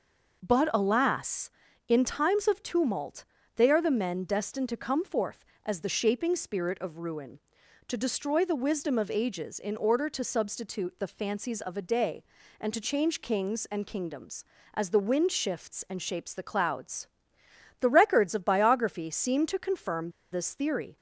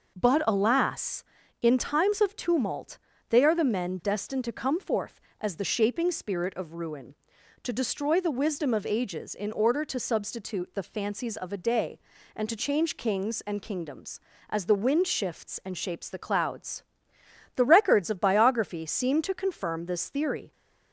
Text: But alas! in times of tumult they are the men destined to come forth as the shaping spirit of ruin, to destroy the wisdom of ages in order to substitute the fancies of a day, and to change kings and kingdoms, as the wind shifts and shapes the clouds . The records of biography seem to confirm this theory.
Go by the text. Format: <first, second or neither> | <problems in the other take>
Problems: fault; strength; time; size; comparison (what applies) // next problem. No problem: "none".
second | pauses between "tumult" and "they"; slight; at 3.2 s; 0.32 s long; slight in the second // pauses between "confirm" and "this"; slight; at 20.0 s; 0.22 s long